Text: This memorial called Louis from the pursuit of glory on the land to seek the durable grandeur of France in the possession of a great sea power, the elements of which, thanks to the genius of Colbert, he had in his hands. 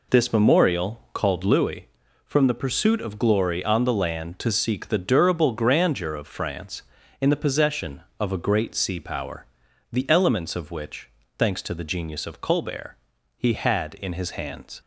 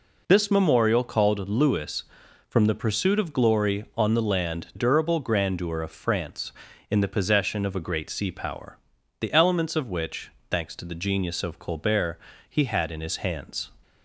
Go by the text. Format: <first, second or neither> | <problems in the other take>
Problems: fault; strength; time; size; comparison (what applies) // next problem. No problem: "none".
first | skips "to seek the"; at 4.7 s